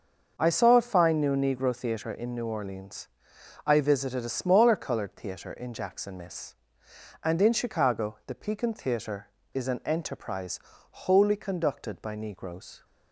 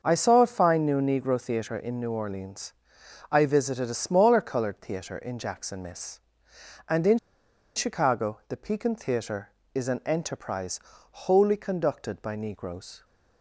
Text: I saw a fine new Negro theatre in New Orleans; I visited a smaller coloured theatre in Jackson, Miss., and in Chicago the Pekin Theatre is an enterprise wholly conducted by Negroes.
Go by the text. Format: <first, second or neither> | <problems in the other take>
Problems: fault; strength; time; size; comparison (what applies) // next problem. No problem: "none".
first | starts louder than the rest; until 1.0 s; 6.5 dB; also in the first // pauses between "in" and "Chicago"; noticeable; at 7.1 s; 0.57 s long // pauses between "enterprise" and "wholly"; slight; at 10.8 s; 0.32 s long; slight in the first